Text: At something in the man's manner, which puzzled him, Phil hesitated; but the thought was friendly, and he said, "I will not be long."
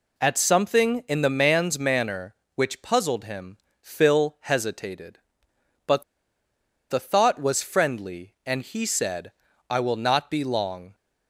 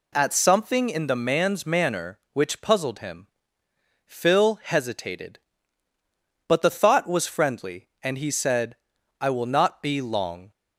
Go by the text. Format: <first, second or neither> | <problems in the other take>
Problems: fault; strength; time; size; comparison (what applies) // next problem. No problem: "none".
second | pauses between "but" and "the"; noticeable; at 6.0 s; 0.87 s long